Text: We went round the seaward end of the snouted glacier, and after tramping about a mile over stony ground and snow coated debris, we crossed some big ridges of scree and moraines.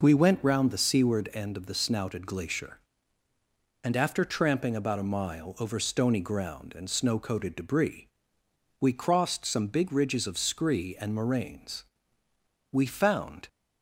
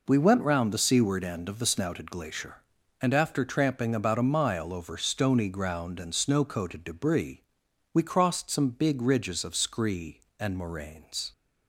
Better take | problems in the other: second | goes on to say "We found"; noticeable; from 12.7 s on; 0.76 s long

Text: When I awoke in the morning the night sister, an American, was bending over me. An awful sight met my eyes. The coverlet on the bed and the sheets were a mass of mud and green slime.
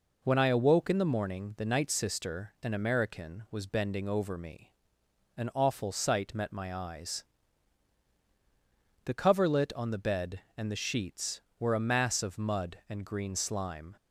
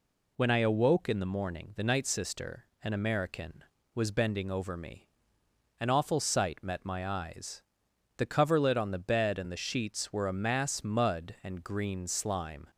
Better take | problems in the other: first | skips "of"; at 10.8 s

